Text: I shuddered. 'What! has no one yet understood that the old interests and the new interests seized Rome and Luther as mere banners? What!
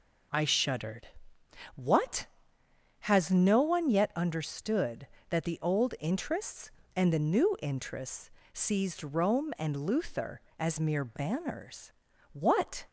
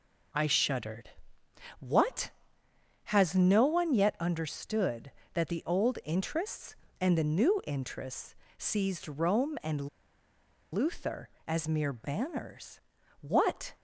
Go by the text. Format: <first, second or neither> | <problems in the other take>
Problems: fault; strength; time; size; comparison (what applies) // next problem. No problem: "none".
first | pauses between "interests" and "seized"; slight; at 8.3 s; 0.24 s long; slight in the first // pauses between "and" and "Luther"; noticeable; at 9.8 s; 0.86 s long